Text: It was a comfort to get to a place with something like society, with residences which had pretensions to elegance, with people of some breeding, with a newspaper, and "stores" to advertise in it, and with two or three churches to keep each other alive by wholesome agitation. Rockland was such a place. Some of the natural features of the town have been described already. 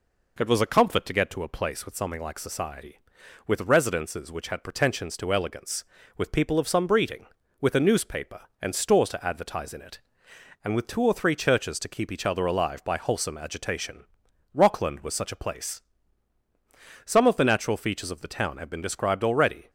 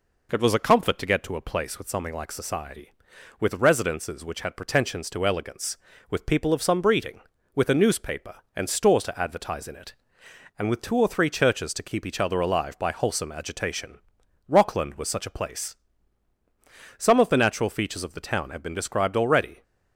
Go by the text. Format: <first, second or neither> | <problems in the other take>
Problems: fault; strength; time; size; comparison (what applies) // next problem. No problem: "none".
neither | none